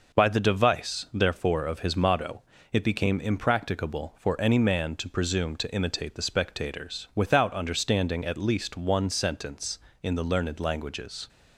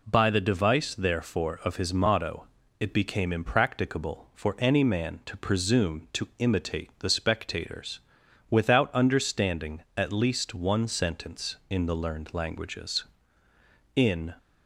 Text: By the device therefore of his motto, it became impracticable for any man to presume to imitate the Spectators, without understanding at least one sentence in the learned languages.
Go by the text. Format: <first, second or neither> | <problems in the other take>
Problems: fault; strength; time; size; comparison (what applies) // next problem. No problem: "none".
first | goes on to say "In"; slight; from 13.9 s on; 0.40 s long